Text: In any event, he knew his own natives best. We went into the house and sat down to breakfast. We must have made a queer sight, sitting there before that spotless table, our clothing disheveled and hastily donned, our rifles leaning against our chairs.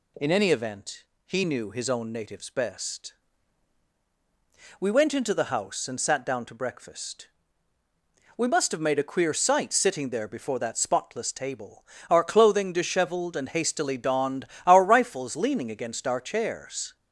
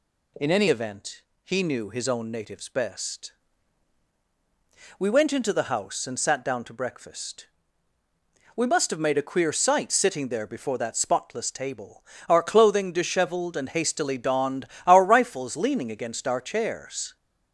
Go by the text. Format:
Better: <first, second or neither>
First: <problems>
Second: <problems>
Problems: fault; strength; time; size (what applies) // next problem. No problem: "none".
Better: neither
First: none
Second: none